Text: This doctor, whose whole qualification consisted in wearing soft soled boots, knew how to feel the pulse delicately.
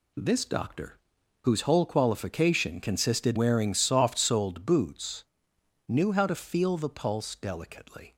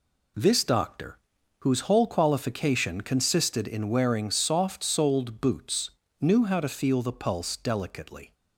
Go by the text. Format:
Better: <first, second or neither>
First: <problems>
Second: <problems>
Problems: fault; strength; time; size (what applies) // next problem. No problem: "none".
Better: second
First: skips "in"; at 3.3 s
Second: none